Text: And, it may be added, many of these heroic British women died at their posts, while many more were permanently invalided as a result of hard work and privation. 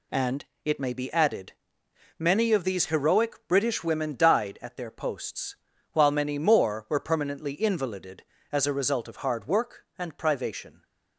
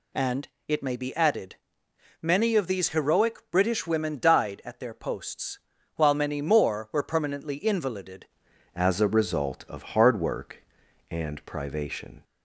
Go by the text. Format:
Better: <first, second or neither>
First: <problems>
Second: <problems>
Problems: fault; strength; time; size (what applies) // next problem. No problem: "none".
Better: first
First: none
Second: changes voice at "as"; from 8.7 s on; 3.5 s long